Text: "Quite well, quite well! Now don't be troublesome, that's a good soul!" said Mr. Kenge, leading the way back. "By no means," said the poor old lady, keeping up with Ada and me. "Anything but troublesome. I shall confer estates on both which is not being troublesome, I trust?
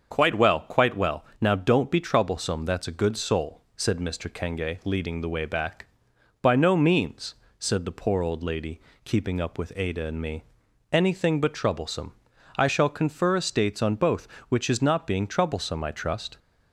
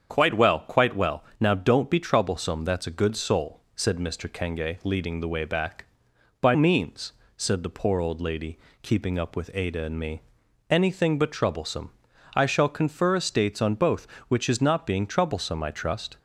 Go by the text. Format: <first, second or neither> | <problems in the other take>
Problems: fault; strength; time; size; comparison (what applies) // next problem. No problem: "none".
first | starts louder than the rest; strong; until 1.1 s; 7.5 dB; also in the first // skips "no"; at 6.5 s